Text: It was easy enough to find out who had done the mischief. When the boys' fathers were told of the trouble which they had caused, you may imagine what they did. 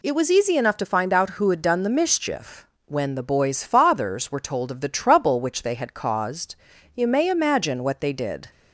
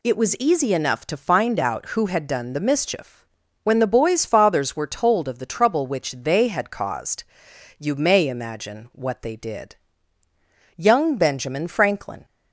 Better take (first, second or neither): first